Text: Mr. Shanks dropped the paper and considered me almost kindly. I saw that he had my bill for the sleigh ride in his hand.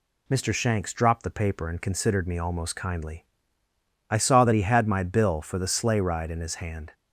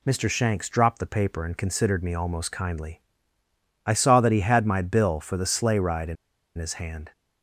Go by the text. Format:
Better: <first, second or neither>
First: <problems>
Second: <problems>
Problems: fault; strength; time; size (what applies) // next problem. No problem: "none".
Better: first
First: none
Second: pauses between "in" and "his"; at 6.1 s; 0.42 s long